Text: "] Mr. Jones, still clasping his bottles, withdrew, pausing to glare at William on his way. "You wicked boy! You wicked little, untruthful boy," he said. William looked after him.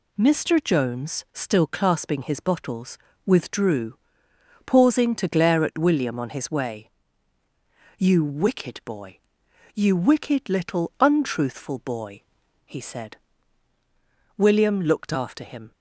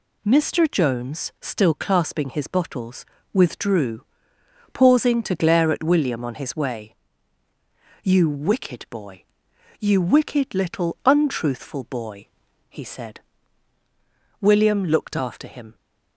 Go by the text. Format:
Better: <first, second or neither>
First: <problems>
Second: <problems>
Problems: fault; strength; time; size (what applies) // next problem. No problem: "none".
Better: neither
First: none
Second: none